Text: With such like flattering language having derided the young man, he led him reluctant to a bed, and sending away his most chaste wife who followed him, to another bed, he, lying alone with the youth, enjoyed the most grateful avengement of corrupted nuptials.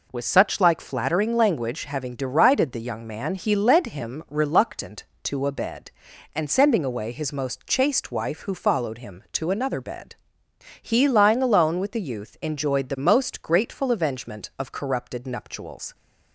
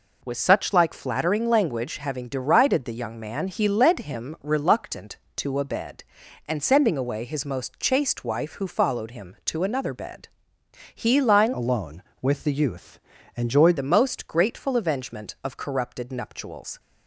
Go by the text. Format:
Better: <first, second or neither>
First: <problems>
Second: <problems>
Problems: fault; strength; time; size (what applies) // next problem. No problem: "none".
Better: first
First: none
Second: changes voice from "alone" to "enjoyed"; from 11.5 to 13.7 s; 2.2 s long